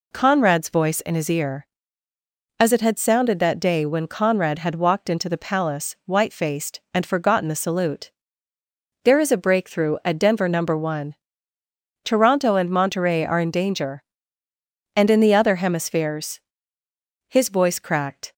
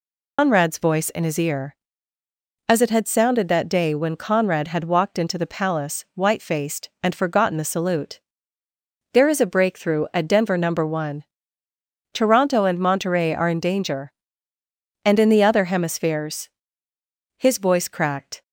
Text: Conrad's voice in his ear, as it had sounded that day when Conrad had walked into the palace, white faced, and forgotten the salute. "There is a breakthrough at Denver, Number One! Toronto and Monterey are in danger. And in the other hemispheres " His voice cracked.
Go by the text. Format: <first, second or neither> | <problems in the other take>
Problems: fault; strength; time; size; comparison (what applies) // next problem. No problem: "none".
first | loses the start of "Conrad's"; at 0.3 s; 165 ms